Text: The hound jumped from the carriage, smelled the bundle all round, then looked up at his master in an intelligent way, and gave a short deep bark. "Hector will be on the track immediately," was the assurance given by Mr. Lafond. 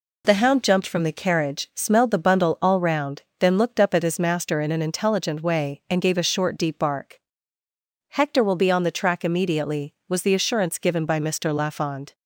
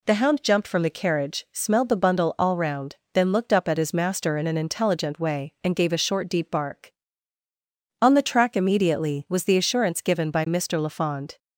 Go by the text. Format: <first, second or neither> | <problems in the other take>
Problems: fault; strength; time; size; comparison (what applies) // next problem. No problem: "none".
first | skips "Hector will be"; at 7.4 s